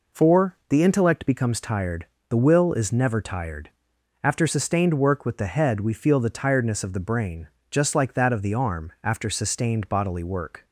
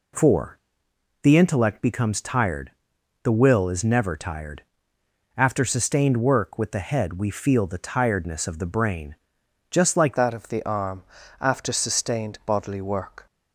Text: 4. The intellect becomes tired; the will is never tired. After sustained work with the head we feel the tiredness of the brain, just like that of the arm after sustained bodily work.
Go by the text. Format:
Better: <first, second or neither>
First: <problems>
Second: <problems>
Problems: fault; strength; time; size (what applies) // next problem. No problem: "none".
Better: first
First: none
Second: changes voice at "that"; from 10.1 s on; 3.1 s long // pauses between "arm" and "after"; slight; at 11.0 s; 0.36 s long